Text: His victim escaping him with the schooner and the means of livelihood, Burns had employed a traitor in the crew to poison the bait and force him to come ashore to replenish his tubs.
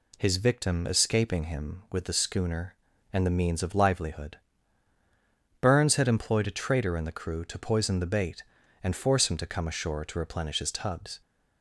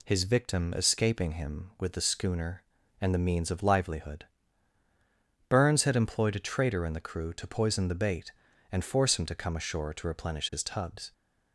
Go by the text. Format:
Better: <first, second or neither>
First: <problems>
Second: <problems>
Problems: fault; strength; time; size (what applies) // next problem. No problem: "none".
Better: neither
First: none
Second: none